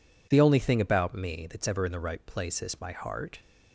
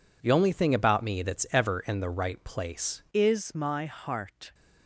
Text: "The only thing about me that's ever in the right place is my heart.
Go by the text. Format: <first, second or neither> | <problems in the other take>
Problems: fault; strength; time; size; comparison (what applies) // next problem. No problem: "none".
first | changes voice at "is"; from 3.1 s on; 1.4 s long